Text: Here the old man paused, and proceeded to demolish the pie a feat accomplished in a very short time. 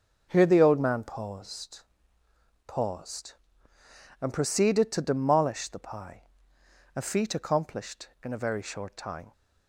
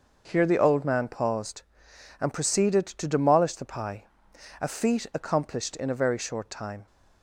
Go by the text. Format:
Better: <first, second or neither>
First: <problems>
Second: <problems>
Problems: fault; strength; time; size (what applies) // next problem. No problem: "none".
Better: second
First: starts louder than the rest; until 1.3 s; 6.5 dB // says "paused" twice; at 2.6 s // pauses between "pie" and "a"; noticeable; at 6.2 s; 0.70 s long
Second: starts louder than the rest; noticeable; until 1.3 s; 6 dB // pauses between "pie" and "a"; noticeable; at 4.0 s; 0.54 s long